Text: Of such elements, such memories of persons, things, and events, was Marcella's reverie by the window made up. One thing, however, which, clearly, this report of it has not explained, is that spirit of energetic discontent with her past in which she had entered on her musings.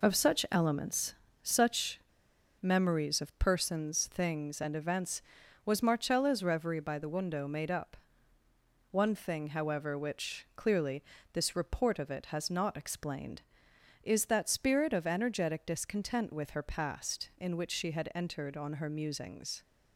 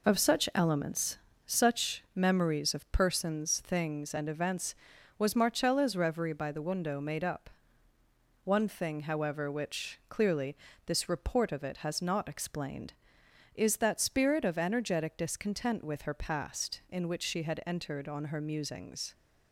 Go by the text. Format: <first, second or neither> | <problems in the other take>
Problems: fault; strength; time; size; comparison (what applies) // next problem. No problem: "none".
second | pauses between "such" and "memories"; noticeable; at 1.9 s; 0.60 s long